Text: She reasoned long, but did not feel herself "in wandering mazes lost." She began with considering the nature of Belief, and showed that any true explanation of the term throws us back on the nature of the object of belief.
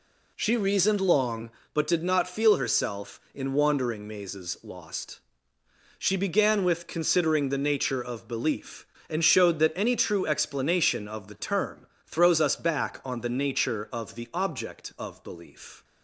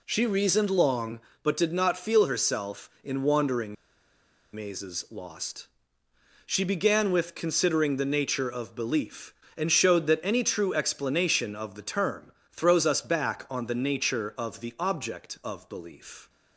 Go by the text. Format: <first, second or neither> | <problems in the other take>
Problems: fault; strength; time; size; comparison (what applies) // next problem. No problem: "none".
first | pauses between "wandering" and "mazes"; noticeable; at 3.7 s; 0.79 s long // pauses between "term" and "throws"; slight; at 12.3 s; 0.20 s long; slight in the first